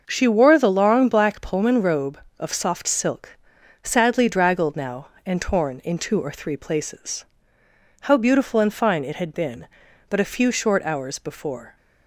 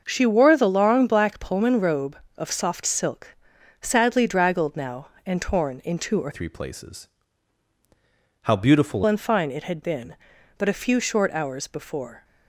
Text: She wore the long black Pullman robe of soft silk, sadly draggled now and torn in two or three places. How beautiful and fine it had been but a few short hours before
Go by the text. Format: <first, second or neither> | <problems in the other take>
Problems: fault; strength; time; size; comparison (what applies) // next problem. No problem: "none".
first | starts louder than the rest; until 1.0 s; 6.5 dB; also in the first // changes voice from "three" to "beautiful"; from 6.3 to 9.0 s; 2.7 s long